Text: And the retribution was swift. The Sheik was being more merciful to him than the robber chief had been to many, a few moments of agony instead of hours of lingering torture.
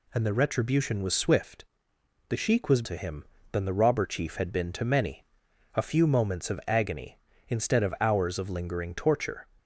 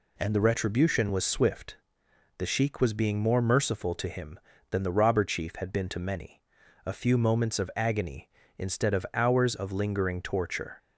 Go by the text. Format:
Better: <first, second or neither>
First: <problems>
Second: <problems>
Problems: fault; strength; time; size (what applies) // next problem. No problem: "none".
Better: second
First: skips "being more merciful"; at 2.8 s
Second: none